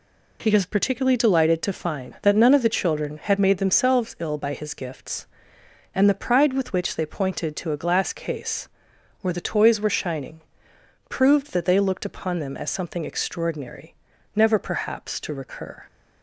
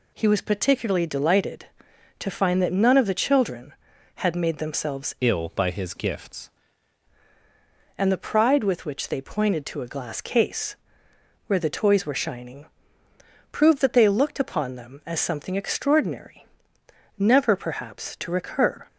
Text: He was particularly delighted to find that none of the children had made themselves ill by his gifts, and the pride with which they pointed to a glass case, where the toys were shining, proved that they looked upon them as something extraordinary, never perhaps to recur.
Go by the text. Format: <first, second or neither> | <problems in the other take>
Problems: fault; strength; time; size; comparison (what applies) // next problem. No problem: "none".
first | changes voice from "ill" to "gifts"; from 5.1 to 6.4 s; 1.3 s long